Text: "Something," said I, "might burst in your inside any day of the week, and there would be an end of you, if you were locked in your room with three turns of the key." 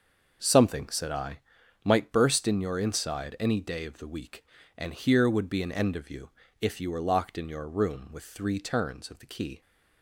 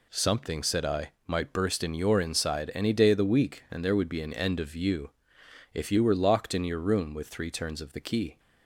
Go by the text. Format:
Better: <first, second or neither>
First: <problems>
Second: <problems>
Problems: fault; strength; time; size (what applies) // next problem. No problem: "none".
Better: second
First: says "here" for "there"; at 4.9 s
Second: none